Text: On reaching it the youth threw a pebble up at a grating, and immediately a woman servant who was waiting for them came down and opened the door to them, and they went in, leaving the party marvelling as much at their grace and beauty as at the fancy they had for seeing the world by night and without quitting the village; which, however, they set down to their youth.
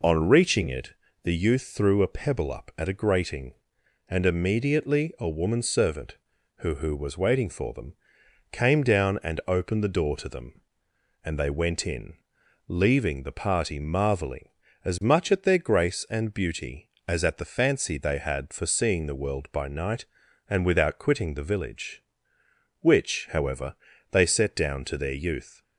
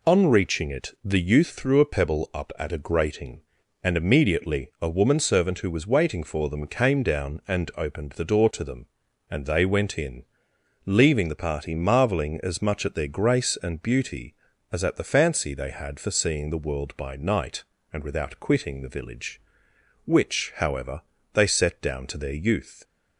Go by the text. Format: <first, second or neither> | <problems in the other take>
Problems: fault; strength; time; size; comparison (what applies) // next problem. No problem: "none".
second | pauses between "it" and "the"; slight; at 0.9 s; 0.28 s long // says "who" twice; at 6.7 s // pauses between "them" and "came"; noticeable; at 7.9 s; 0.58 s long